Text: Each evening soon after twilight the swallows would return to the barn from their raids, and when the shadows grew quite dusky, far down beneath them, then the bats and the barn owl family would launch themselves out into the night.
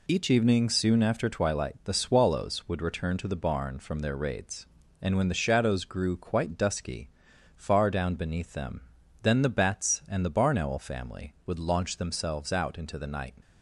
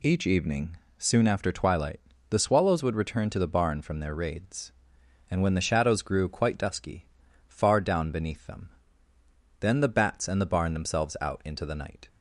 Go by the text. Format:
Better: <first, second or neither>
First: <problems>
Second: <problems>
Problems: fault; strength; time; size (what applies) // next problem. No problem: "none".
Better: first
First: none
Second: pauses between "evening" and "soon"; slight; at 0.7 s; 0.22 s long // pauses between "twilight" and "the"; slight; at 1.9 s; 0.30 s long // skips "owl family would launch"; at 10.7 s